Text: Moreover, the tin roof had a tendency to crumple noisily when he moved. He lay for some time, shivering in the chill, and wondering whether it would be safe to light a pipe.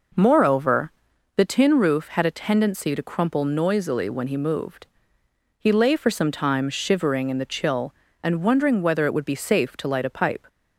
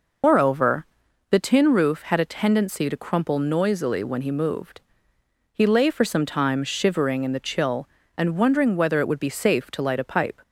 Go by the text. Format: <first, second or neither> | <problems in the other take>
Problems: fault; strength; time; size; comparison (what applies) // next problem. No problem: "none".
first | loses the start of "Moreover"; at 0.2 s; 180 ms